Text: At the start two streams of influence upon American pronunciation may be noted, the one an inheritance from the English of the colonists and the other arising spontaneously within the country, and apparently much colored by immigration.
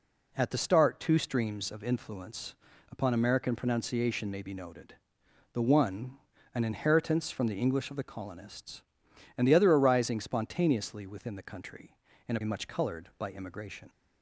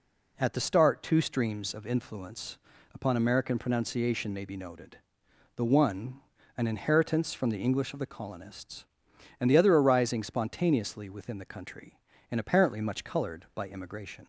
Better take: second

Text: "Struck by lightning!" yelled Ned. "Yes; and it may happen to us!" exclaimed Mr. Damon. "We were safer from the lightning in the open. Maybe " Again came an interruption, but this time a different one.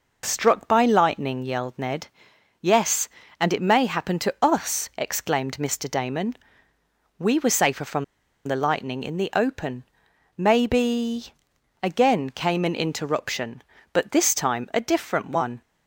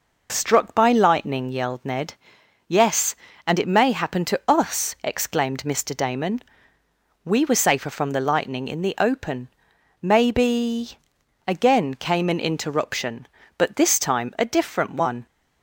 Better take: second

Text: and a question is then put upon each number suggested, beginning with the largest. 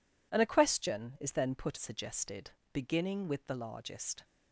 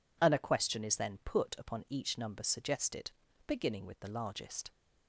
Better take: second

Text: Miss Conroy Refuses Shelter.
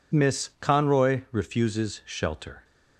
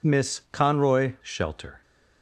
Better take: first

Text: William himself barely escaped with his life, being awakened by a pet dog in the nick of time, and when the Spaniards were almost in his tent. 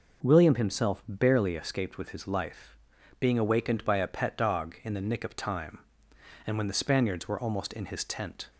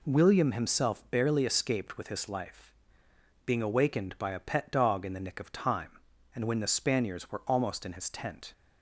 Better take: neither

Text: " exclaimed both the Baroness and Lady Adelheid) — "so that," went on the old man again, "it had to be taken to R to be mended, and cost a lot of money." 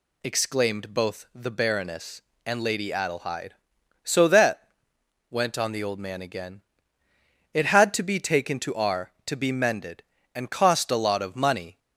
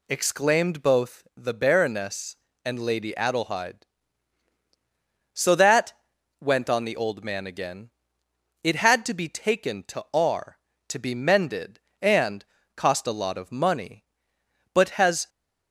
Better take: first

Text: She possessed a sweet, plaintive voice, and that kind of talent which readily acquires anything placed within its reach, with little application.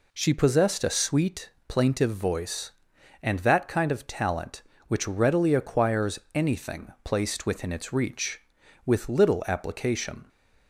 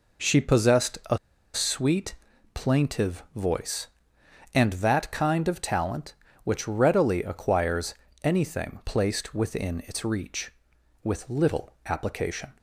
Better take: first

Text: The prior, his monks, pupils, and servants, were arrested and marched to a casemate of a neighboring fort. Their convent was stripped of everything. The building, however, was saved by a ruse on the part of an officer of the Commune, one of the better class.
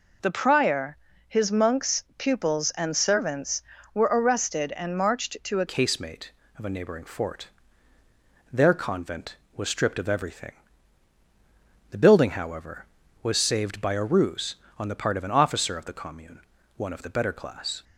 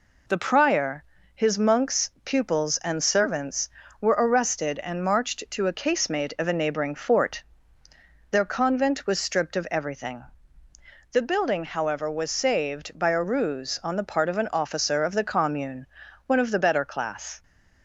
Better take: second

